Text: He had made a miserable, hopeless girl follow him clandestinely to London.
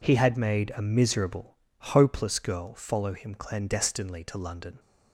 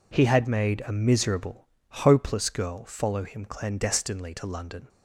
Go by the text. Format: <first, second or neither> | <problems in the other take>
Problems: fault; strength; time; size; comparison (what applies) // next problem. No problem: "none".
neither | none